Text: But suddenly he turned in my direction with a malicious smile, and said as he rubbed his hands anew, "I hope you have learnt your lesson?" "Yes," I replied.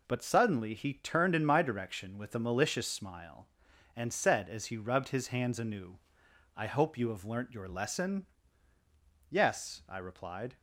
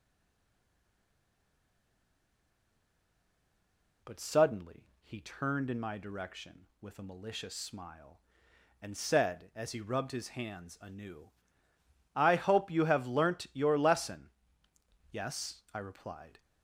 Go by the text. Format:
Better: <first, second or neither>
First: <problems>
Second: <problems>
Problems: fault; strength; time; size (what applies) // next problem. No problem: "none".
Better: first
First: none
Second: stays silent before the first word; strong; until 4.0 s; 4.0 s long // pauses between "suddenly" and "he"; slight; at 4.8 s; 0.16 s long